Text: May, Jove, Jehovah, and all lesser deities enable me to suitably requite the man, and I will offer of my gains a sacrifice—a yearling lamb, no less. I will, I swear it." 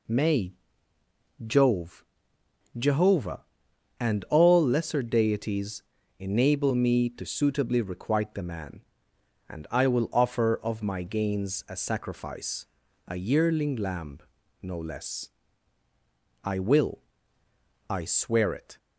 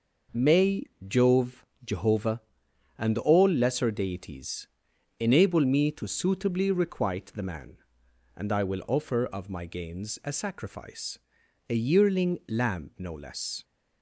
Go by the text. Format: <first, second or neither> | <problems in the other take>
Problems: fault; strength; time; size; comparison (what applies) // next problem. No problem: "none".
first | pauses between "deities" and "enable"; noticeable; at 4.6 s; 0.50 s long; slight in the first // stops before "I will I swear it"; at 13.6 s